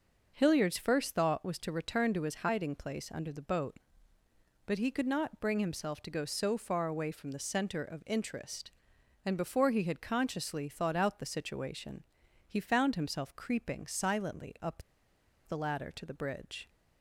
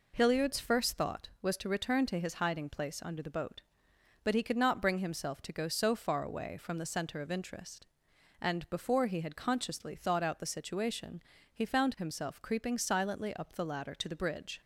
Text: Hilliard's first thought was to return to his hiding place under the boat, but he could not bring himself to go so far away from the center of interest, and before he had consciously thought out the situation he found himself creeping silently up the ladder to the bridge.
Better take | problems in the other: second | pauses between "situation" and "he"; at 12.0 s; 0.44 s long; slight in the second // pauses between "up" and "the"; noticeable; at 14.8 s; 0.64 s long

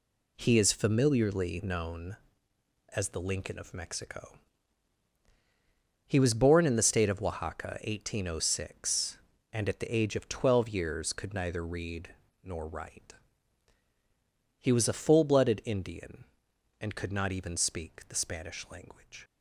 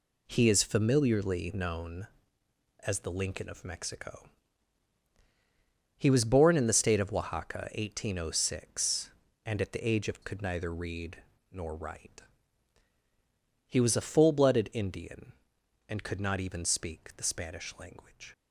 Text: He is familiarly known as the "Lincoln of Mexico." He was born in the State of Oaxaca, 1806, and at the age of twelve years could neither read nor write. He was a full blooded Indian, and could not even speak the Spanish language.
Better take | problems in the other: first | skips "twelve years"; at 10.2 s // pauses between "read" and "nor"; slight; at 11.1 s; 0.32 s long; slight in the first

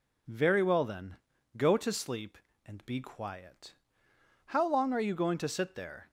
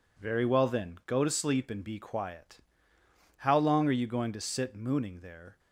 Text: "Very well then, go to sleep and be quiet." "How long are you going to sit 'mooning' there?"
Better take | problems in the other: second | skips "mooning"; at 5.7 s

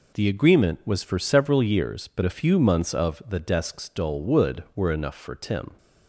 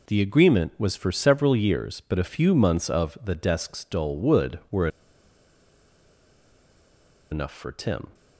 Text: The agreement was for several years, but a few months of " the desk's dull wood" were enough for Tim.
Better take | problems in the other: first | pauses between "were" and "enough"; strong; at 4.8 s; 2.4 s long

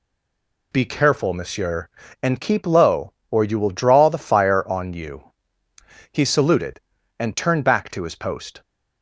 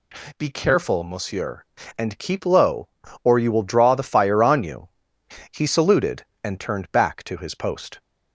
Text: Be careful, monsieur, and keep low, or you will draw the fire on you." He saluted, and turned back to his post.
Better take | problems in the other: second | stays silent before the first word; slight; until 0.7 s; 0.7 s long

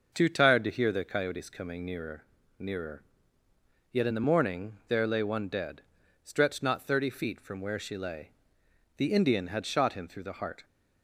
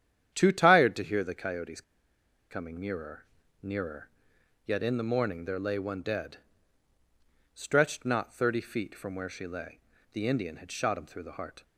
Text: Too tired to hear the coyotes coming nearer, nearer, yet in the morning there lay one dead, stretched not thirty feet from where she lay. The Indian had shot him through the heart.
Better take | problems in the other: first | starts louder than the rest; strong; until 1.3 s; 9.5 dB; also in the first // pauses between "coyotes" and "coming"; noticeable; at 1.8 s; 0.68 s long

